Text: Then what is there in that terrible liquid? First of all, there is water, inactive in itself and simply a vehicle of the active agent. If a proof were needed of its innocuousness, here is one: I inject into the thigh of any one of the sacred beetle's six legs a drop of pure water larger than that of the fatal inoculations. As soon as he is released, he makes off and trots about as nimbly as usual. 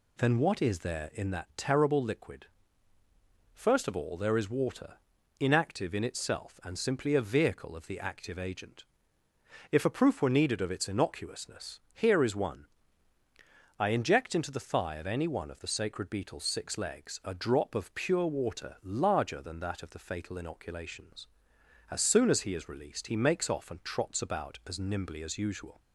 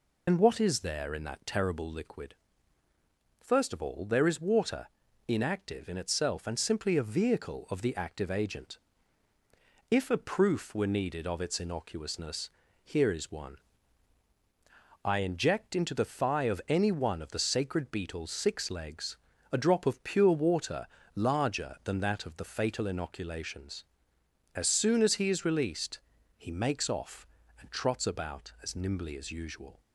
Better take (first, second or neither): first